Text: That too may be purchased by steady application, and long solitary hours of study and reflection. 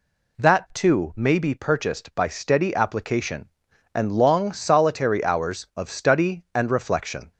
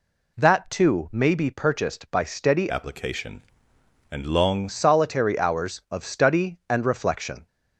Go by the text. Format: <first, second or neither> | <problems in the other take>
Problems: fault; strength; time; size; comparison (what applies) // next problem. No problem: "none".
first | changes voice from "application" to "long"; from 2.6 to 4.6 s; 2.0 s long